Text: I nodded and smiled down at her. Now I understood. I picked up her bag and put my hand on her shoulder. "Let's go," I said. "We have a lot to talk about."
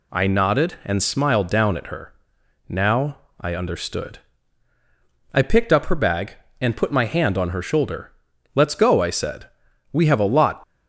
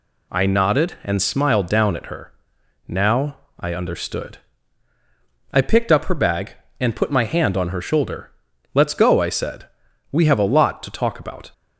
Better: second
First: pauses between "Now" and "I"; slight; at 3.1 s; 0.22 s long // stops before "to talk about"; at 10.6 s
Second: pauses between "Now" and "I"; slight; at 3.3 s; 0.22 s long

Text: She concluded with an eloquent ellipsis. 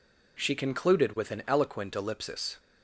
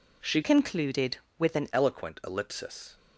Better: first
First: none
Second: changes voice from "concluded" to "an"; from 0.4 to 1.6 s; 1.2 s long

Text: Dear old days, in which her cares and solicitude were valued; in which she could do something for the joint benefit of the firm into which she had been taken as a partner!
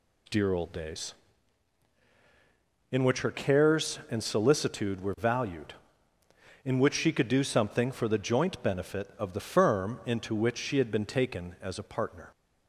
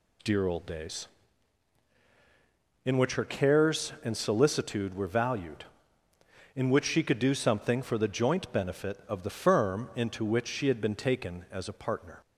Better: neither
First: none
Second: none

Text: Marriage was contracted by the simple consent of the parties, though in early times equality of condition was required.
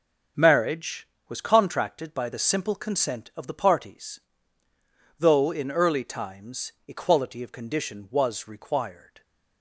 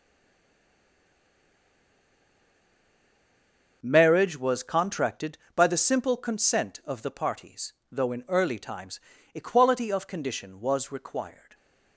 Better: first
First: starts louder than the rest; until 1.6 s; 6.5 dB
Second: stays silent before the first word; strong; until 3.8 s; 3.8 s long // starts louder than the rest; until 4.8 s; 6.5 dB // pauses between "times" and "equality"; slight; at 8.9 s; 0.36 s long

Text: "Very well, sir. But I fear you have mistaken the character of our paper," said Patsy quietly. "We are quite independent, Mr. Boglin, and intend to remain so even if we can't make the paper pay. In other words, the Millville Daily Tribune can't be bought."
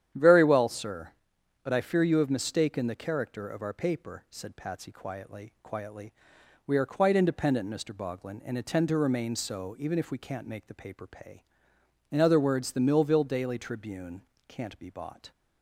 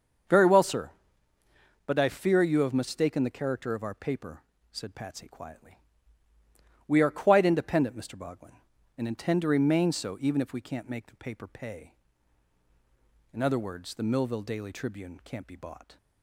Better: second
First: starts louder than the rest; strong; until 1.6 s; 10 dB // says "quietly" twice; at 5.6 s // pauses between "Tribune" and "can't"; slight; at 14.2 s; 0.26 s long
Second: starts louder than the rest; until 2.2 s; 6.5 dB

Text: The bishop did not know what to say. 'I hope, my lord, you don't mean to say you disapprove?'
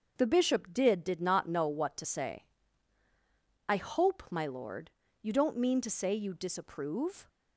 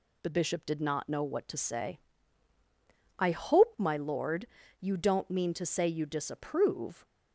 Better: second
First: starts louder than the rest; until 1.1 s; 6 dB // says "did" twice; at 1.0 s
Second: none

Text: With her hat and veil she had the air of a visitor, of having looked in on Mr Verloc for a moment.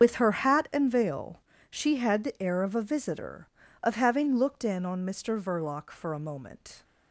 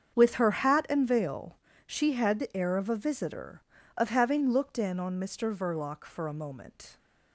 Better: second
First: loses the start of "With"; at 0.0 s; 45 ms // starts louder than the rest; strong; until 1.0 s; 7.5 dB // pauses between "veil" and "she"; slight; at 1.4 s; 0.30 s long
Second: starts louder than the rest; strong; until 1.2 s; 7.5 dB // pauses between "veil" and "she"; slight; at 1.5 s; 0.30 s long

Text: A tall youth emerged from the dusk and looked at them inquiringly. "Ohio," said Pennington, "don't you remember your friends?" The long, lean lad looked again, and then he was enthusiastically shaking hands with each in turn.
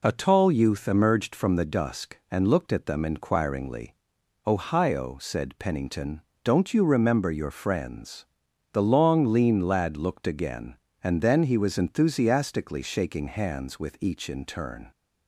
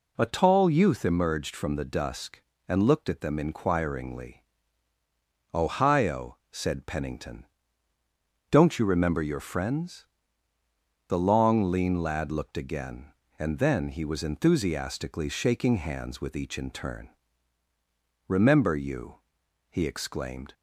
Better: first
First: none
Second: goes on to say "Remember you he exclaimed"; strong; from 18.2 s on; 2.2 s long

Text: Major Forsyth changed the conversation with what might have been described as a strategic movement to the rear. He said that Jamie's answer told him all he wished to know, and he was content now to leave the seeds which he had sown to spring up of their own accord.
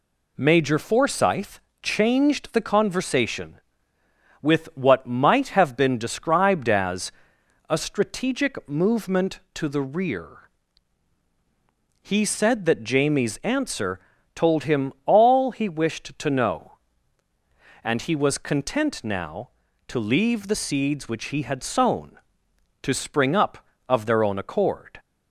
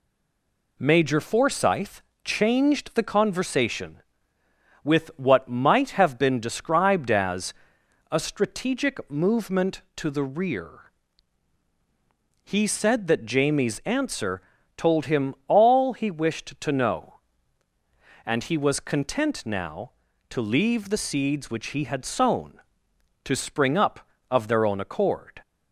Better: first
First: pauses between "Forsyth" and "changed"; slight; at 1.5 s; 0.22 s long // pauses between "as" and "a"; noticeable; at 7.0 s; 0.60 s long // pauses between "answer" and "told"; slight; at 13.9 s; 0.36 s long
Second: stays silent before the first word; slight; until 0.7 s; 0.7 s long // pauses between "Forsyth" and "changed"; slight; at 2.0 s; 0.22 s long // pauses between "as" and "a"; noticeable; at 7.5 s; 0.60 s long // pauses between "answer" and "told"; slight; at 14.4 s; 0.36 s long

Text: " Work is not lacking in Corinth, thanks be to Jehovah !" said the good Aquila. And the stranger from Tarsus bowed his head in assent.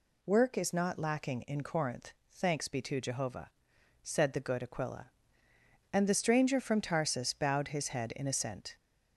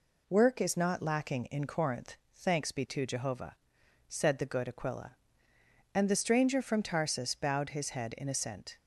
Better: second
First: gets louder; noticeable; throughout; 4.5 dB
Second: none

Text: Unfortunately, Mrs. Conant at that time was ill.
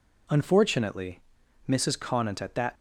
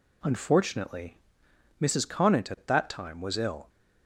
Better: second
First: stops before "time was ill"; at 2.7 s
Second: none

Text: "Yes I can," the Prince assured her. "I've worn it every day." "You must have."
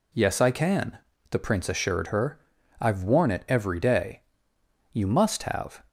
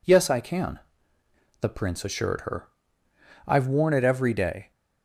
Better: first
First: none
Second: stops before "You must have"; at 4.7 s

